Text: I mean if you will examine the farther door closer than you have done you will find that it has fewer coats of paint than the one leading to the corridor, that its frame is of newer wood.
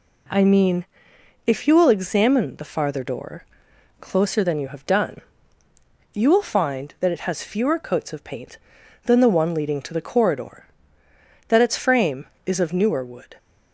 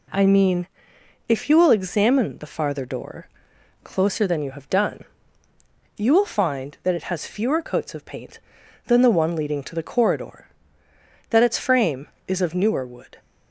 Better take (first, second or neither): neither